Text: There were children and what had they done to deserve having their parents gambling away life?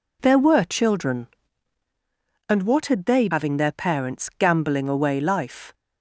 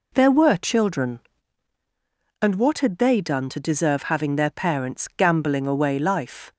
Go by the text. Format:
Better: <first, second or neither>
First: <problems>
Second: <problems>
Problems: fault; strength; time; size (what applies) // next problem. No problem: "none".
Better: second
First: skips "done to deserve"; at 3.2 s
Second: none